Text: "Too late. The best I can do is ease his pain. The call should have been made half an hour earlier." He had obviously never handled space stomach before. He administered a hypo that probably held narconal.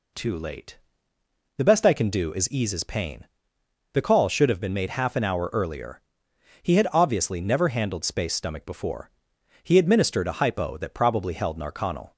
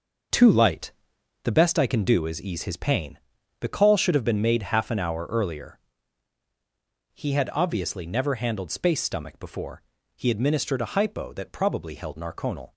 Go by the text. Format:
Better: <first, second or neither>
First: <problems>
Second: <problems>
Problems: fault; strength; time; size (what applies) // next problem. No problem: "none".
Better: first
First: none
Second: starts louder than the rest; until 1.8 s; 6 dB // says "light" for "late"; at 0.5 s